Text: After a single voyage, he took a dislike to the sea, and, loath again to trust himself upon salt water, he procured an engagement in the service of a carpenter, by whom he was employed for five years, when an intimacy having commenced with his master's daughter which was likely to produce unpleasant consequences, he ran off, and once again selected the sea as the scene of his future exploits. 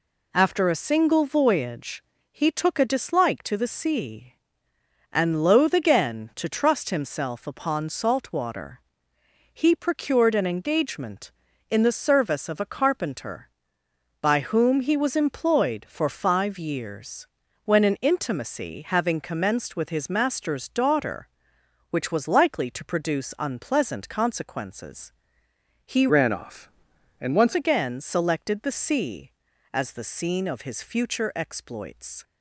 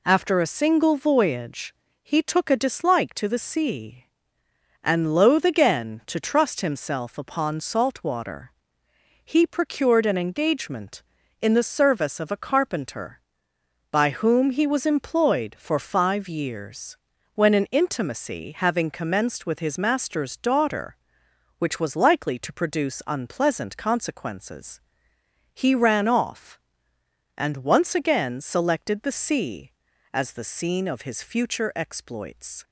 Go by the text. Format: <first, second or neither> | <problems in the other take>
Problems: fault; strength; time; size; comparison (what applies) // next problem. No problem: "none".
second | changes voice from "ran" to "once"; from 26.0 to 27.5 s; 1.5 s long